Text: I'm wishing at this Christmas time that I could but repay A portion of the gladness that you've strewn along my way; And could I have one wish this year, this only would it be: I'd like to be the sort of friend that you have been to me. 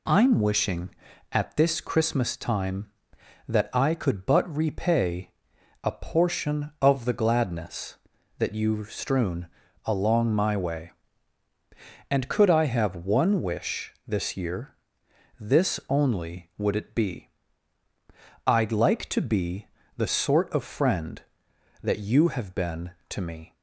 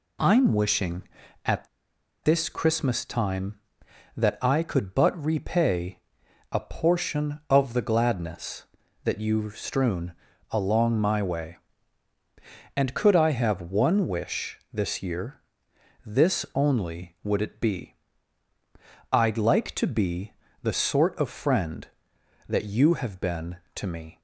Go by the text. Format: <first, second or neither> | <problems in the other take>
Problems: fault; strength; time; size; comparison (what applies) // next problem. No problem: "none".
first | pauses between "at" and "this"; noticeable; at 1.6 s; 0.57 s long // pauses between "repay" and "A"; noticeable; at 6.0 s; 0.50 s long; noticeable in the first // pauses between "strewn" and "along"; at 10.1 s; 0.38 s long; also in the first // pauses between "be" and "the"; slight; at 20.3 s; 0.28 s long; slight in the first